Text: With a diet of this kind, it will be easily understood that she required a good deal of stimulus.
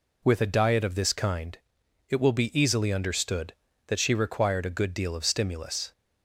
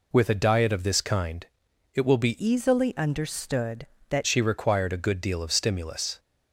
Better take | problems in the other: first | changes voice from "easily" to "that"; from 2.3 to 4.2 s; 1.9 s long

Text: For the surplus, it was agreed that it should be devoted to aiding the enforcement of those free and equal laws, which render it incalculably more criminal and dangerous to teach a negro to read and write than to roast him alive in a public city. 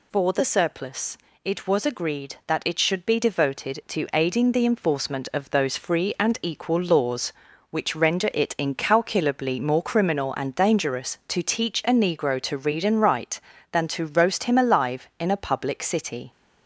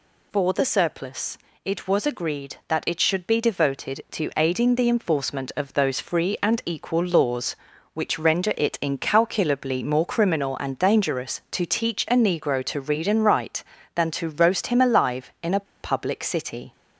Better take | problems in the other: first | pauses between "a" and "public"; slight; at 15.6 s; 0.17 s long

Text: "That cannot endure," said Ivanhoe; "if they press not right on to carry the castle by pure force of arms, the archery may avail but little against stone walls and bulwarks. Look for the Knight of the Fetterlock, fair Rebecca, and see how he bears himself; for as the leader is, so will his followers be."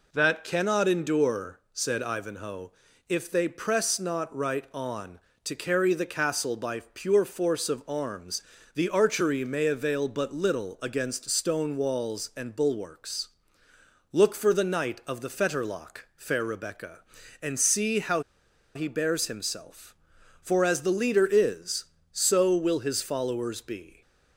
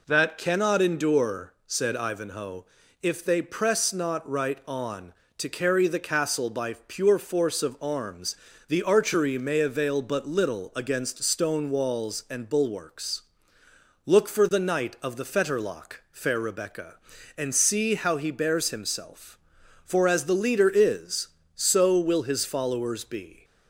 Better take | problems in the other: second | pauses between "how" and "he"; noticeable; at 18.2 s; 0.54 s long

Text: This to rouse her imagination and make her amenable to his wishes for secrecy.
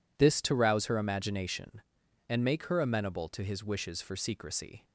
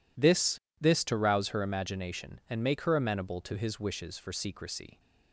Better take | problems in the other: first | says "This" twice; at 0.7 s

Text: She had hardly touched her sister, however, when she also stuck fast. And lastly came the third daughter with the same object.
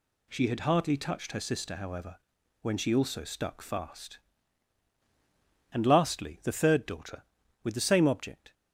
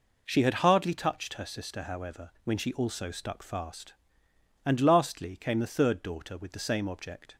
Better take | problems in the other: second | skips "came"; at 6.4 s

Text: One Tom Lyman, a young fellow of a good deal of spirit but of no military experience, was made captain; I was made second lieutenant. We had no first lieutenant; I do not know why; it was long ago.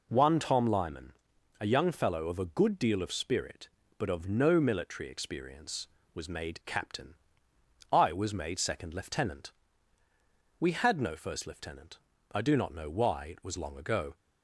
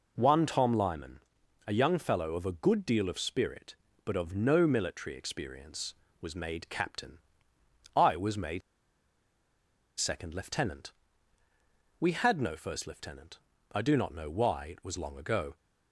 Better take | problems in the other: first | pauses between "made" and "second"; strong; at 8.6 s; 1.3 s long

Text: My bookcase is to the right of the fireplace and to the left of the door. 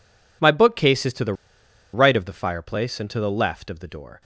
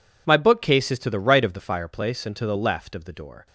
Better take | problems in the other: second | pauses between "the" and "right"; noticeable; at 1.3 s; 0.60 s long

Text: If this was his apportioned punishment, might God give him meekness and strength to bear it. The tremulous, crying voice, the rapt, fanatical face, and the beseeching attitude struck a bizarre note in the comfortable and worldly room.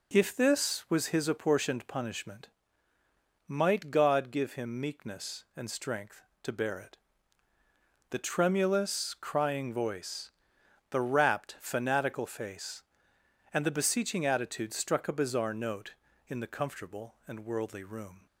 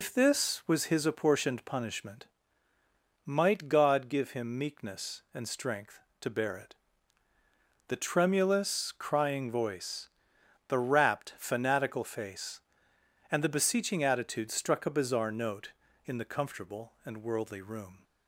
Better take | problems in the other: first | loses the start of "If"; at 0.0 s; 120 ms

